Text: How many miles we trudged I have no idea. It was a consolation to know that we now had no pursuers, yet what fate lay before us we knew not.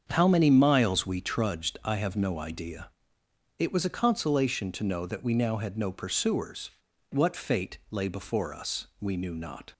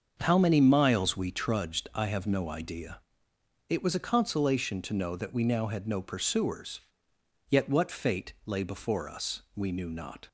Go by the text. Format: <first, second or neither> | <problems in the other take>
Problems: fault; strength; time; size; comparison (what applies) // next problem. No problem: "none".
second | starts louder than the rest; strong; until 1.1 s; 7.5 dB; also in the second // skips "yet"; at 6.9 s